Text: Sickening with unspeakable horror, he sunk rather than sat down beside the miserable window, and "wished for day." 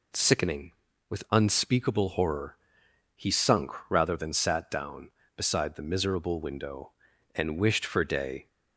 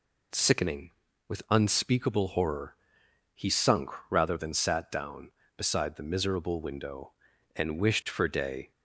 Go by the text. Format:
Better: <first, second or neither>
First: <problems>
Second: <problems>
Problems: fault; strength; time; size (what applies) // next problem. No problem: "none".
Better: neither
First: pauses between "sunk" and "rather"; slight; at 3.7 s; 0.18 s long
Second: pauses between "sunk" and "rather"; slight; at 3.8 s; 0.20 s long